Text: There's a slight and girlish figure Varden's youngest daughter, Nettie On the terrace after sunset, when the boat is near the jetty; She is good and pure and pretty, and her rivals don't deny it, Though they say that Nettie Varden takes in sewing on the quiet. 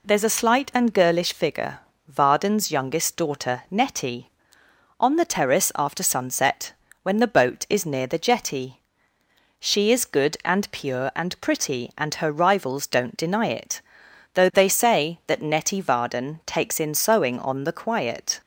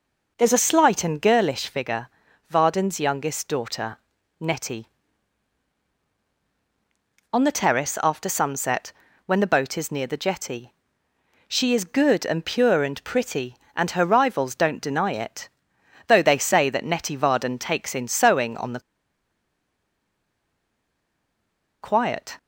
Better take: first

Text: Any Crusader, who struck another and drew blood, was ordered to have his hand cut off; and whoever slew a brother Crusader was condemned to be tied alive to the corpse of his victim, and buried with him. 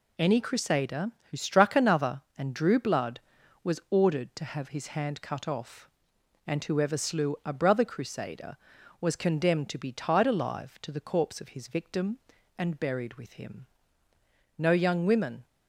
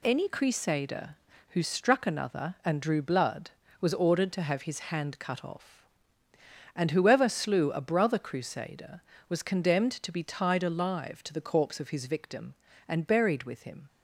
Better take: second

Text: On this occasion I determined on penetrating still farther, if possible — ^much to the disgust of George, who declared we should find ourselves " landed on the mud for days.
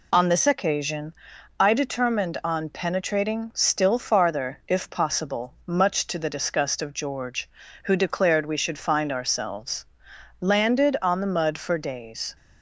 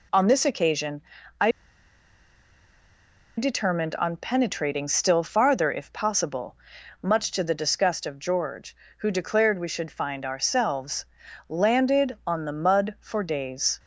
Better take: first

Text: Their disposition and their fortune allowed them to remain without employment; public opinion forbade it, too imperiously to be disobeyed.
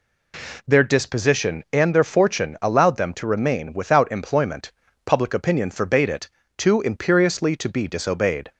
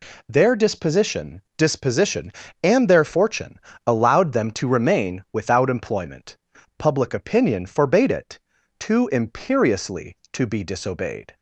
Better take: first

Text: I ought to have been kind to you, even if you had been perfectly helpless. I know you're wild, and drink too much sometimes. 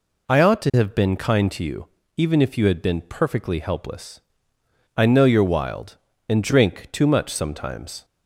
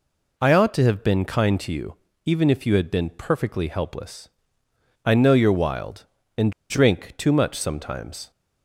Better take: first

